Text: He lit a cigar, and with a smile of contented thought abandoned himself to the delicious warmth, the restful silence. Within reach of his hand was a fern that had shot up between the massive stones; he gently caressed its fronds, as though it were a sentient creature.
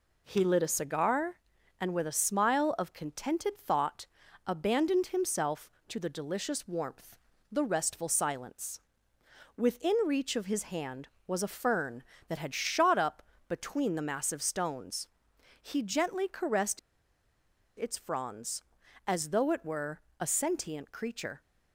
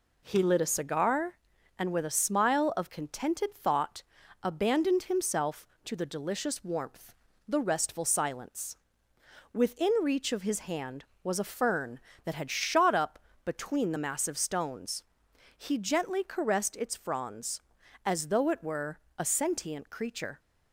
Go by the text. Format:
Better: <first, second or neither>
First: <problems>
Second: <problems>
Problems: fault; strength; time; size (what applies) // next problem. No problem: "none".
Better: second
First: pauses between "thought" and "abandoned"; at 4.0 s; 0.40 s long // pauses between "up" and "between"; slight; at 13.2 s; 0.26 s long // pauses between "caressed" and "its"; at 16.7 s; 0.99 s long // pauses between "were" and "a"; slight; at 20.0 s; 0.18 s long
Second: pauses between "thought" and "abandoned"; at 4.0 s; 0.40 s long // pauses between "up" and "between"; slight; at 13.1 s; 0.26 s long // pauses between "were" and "a"; slight; at 18.9 s; 0.18 s long